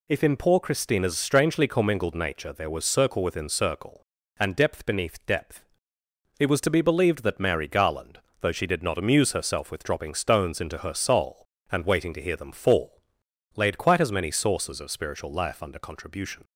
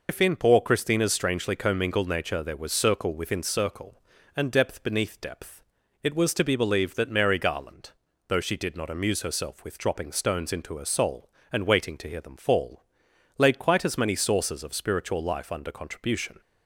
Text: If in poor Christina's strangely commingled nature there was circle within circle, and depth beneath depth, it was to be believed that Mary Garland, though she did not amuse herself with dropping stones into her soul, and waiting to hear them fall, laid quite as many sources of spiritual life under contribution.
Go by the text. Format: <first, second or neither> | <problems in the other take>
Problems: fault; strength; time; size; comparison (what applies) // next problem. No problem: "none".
first | loses the start of "If"; at 0.0 s; 110 ms